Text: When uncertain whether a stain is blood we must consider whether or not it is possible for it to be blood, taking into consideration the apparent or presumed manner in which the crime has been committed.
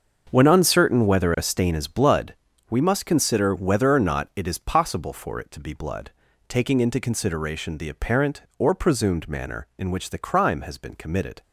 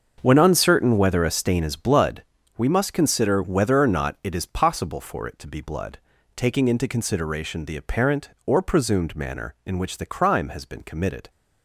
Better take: neither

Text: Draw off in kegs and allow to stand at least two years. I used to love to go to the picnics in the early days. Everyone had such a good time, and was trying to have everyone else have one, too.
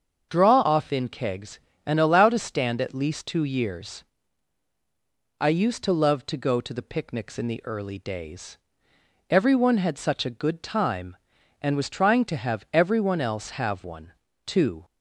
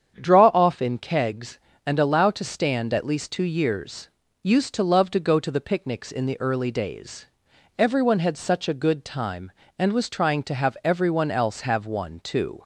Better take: first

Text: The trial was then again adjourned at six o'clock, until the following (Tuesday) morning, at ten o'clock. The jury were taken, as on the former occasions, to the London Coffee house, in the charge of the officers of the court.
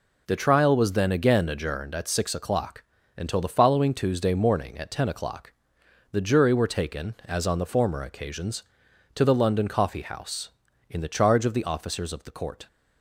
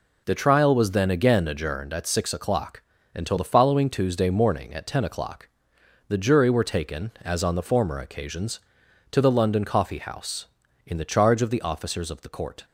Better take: neither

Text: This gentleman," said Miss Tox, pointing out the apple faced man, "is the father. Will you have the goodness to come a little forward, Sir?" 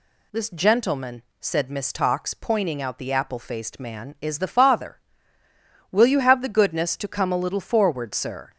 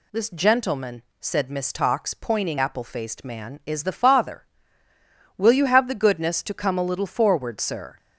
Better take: first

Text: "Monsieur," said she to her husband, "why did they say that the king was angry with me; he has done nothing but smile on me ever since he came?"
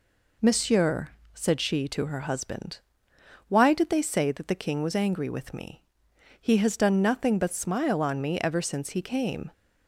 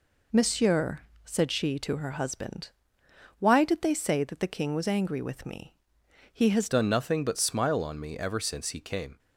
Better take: first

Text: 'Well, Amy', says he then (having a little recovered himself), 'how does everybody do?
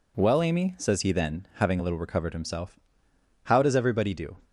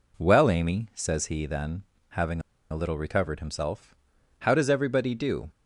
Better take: first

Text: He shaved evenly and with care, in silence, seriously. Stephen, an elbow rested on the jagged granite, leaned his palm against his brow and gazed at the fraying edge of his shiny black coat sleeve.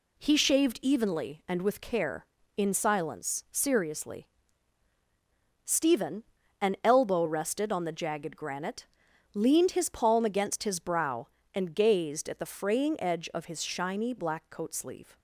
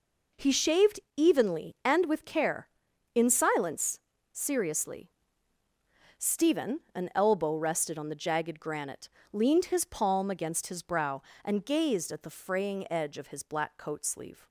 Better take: first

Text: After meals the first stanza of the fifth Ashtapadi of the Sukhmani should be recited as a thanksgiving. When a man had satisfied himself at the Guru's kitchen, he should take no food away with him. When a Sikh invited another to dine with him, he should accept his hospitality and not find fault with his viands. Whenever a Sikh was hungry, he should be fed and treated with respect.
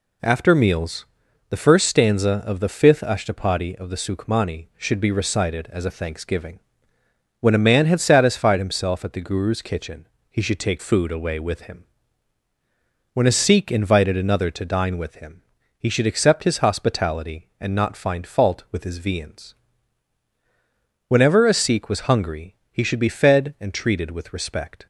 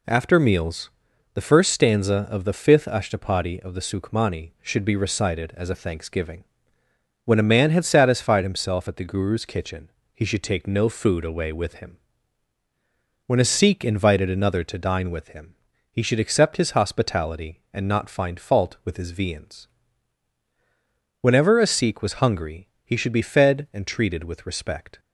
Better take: second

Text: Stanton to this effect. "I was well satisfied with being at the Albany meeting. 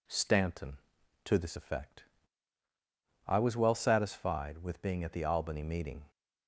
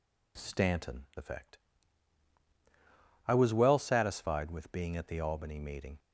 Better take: first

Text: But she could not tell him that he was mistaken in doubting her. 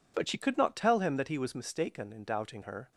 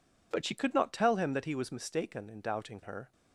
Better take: neither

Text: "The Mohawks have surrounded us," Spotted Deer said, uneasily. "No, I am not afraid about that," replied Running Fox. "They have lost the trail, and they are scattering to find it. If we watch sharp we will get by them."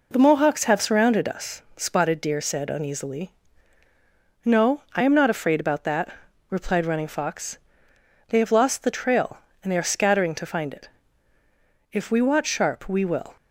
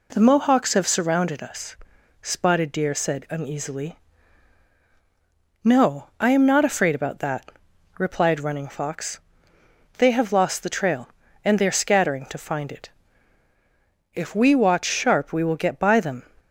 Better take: second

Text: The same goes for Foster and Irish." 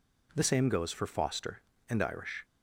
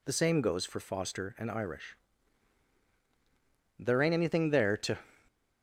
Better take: first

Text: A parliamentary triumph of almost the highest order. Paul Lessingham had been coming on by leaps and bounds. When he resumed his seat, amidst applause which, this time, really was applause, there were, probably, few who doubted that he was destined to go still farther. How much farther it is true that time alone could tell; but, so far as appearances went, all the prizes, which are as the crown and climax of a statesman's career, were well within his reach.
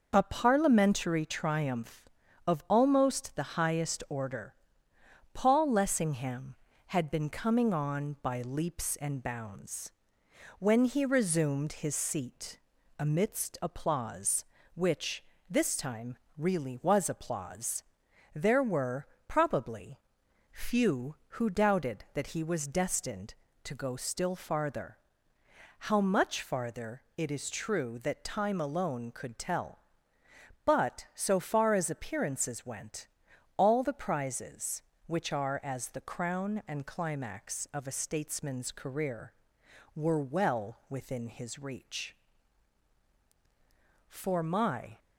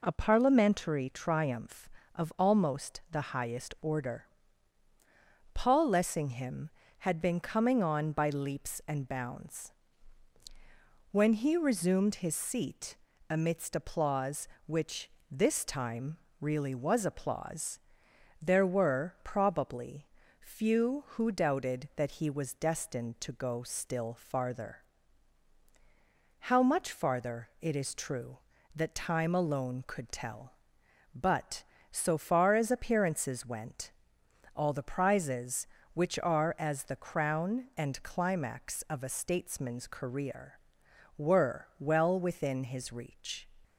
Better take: second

